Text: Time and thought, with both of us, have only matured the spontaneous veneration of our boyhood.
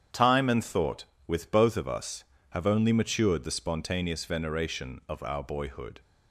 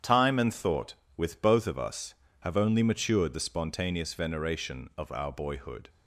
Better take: neither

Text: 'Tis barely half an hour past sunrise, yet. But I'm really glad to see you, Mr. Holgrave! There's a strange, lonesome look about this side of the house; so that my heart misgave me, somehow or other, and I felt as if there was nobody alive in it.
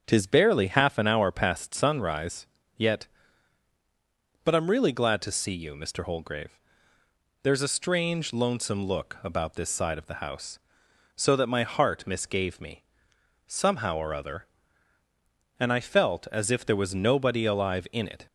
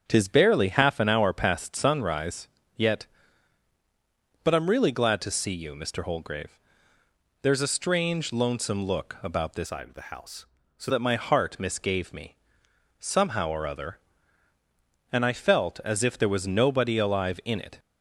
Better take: first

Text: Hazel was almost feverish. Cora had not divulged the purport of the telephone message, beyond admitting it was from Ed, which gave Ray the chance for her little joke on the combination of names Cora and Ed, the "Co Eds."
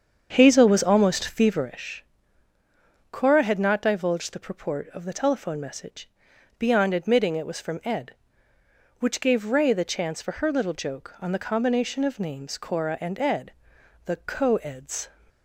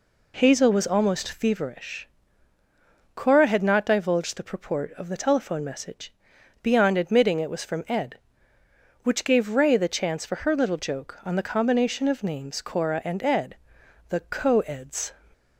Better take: second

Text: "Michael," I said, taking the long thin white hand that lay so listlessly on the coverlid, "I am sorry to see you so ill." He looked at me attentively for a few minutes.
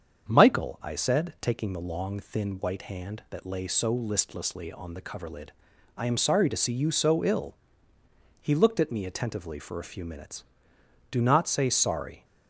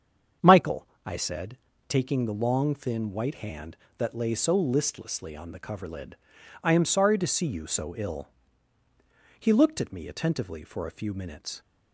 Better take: second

